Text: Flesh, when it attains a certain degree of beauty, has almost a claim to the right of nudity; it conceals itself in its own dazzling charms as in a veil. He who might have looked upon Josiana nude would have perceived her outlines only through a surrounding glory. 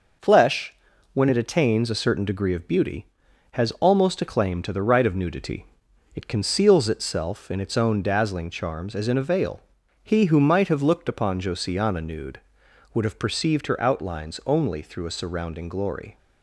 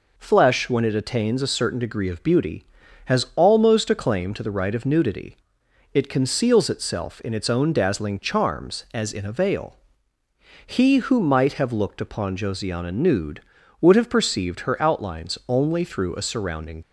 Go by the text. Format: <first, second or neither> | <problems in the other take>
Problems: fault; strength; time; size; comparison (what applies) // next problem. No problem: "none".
first | stops before "glory"; at 16.8 s